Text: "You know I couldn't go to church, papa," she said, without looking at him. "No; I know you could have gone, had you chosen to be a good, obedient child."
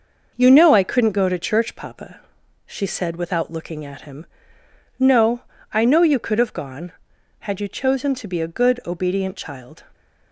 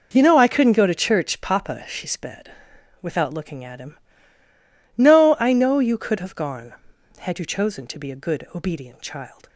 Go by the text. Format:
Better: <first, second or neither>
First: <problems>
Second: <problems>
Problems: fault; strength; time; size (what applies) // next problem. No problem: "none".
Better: first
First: none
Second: says "sped" for "said"; at 2.0 s